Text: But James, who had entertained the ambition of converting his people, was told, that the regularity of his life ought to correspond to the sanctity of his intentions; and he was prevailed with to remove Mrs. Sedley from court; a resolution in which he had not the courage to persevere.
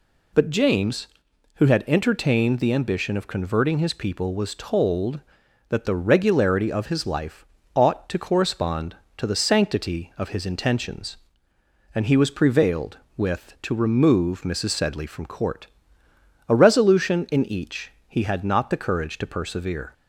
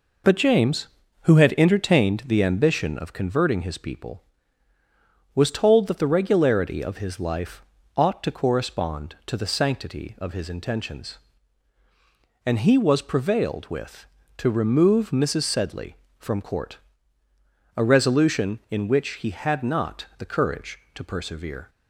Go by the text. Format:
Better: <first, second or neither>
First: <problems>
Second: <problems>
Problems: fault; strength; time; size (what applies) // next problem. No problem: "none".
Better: second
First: pauses between "life" and "ought"; slight; at 7.4 s; 0.26 s long // says "each" for "which"; at 17.4 s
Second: pauses between "life" and "ought"; slight; at 7.6 s; 0.34 s long